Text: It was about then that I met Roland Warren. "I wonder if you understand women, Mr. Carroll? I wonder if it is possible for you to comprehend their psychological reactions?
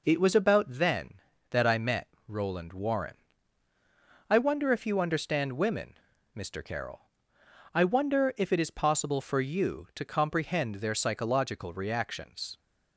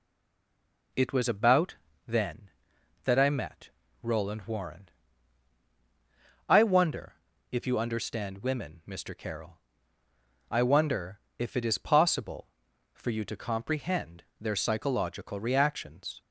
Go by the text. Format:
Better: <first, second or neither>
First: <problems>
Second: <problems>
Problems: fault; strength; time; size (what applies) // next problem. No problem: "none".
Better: first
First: pauses between "met" and "Roland"; slight; at 2.0 s; 0.18 s long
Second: stays silent before the first word; slight; until 0.9 s; 0.9 s long // pauses between "about" and "then"; slight; at 1.7 s; 0.30 s long // pauses between "met" and "Roland"; slight; at 3.7 s; 0.32 s long // pauses between "wonder" and "if"; slight; at 7.1 s; 0.36 s long // pauses between "wonder" and "if"; slight; at 11.1 s; 0.20 s long